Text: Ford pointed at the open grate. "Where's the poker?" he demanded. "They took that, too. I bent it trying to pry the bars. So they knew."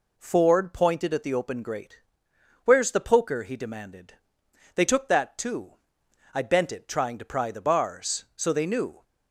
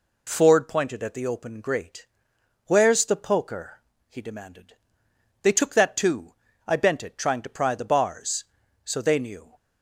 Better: neither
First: none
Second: none

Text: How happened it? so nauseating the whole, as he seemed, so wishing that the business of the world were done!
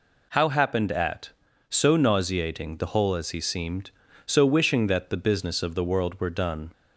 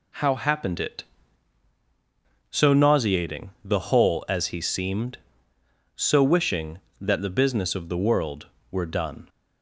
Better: second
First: says "at" for "it"; at 0.9 s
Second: none

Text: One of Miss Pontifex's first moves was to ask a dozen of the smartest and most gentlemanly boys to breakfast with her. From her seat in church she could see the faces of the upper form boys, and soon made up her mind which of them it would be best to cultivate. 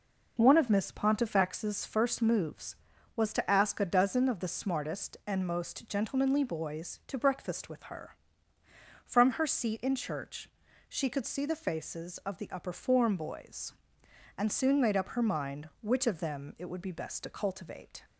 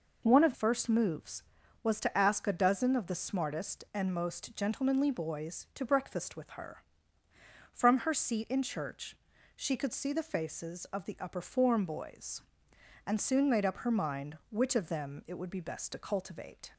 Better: first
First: pauses between "church" and "she"; at 10.4 s; 0.40 s long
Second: skips "Miss Pontifex's"; at 0.5 s // pauses between "church" and "she"; at 9.1 s; 0.40 s long

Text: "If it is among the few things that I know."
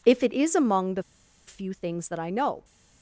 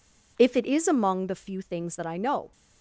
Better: second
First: pauses between "the" and "few"; at 1.0 s; 0.45 s long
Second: none

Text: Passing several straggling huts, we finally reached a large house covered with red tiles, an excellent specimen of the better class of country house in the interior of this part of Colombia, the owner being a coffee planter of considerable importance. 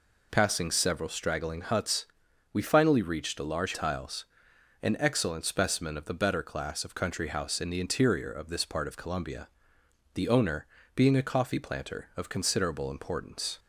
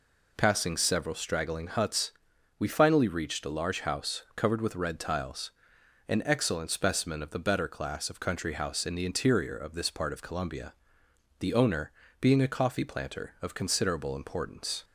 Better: second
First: skips "house covered with red"; at 3.7 s // pauses between "owner" and "being"; slight; at 10.6 s; 0.30 s long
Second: pauses between "owner" and "being"; slight; at 11.9 s; 0.30 s long

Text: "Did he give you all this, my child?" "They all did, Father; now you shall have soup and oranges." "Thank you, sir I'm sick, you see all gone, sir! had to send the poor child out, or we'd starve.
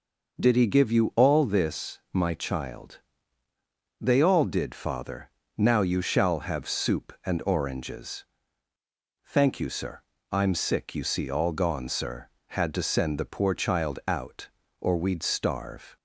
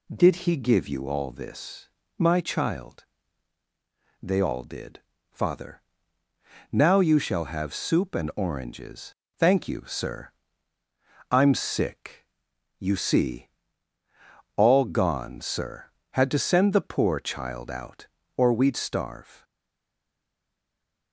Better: first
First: pauses between "sir" and "I'm"; slight; at 10.0 s; 0.28 s long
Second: pauses between "sir" and "I'm"; at 10.2 s; 1.0 s long // pauses between "see" and "all"; at 13.4 s; 1.0 s long // stays silent after the last word; noticeable; from 19.4 s on; 1.7 s long

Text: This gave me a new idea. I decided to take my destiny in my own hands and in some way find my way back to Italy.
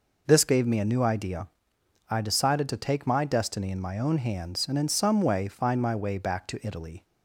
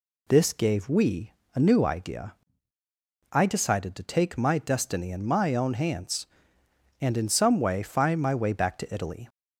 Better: first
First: none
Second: says "we" for "me"; at 0.8 s

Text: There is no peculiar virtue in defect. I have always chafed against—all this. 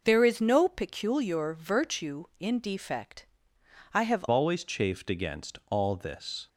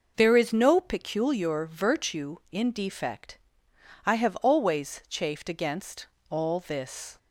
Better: second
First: changes voice at "always"; from 4.2 s on; 2.2 s long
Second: none

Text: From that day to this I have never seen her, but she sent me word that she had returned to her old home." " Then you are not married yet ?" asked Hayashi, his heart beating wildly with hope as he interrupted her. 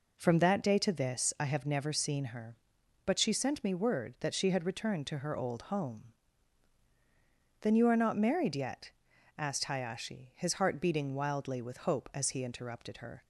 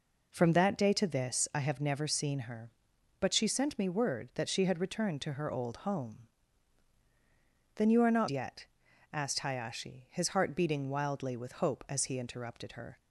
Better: first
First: none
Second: skips "married"; at 8.2 s

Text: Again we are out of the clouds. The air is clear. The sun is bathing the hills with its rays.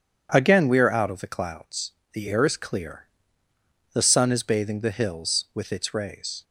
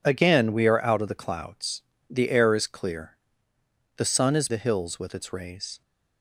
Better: first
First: none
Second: skips "bathing"; at 4.4 s

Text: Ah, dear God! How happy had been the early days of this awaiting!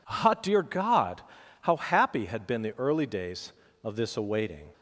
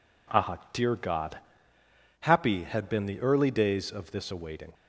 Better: first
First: none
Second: skips "How"; at 1.7 s

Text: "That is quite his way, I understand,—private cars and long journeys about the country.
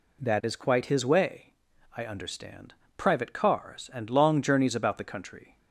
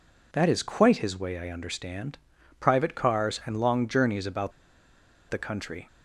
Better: first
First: none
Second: pauses between "about" and "the"; noticeable; at 4.5 s; 0.78 s long

